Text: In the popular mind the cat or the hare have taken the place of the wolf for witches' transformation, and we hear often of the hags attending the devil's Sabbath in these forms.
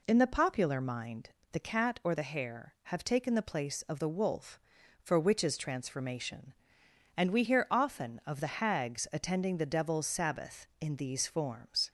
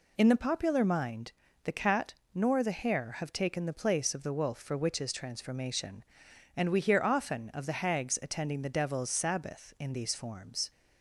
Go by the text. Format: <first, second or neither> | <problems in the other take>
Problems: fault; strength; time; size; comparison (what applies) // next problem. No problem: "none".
first | pauses between "mind" and "the"; slight; at 1.3 s; 0.32 s long; slight in the first // says "nor" for "or"; at 2.3 s